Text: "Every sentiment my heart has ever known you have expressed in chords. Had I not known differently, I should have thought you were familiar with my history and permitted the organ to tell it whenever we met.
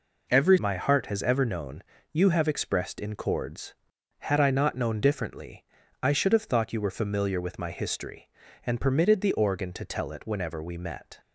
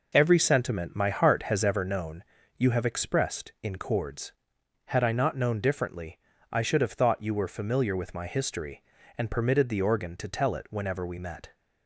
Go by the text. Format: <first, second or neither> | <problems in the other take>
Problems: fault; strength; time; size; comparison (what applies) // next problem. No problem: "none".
second | skips "sentiment"; at 0.5 s // pauses between "known" and "you"; slight; at 1.8 s; 0.30 s long; slight in the second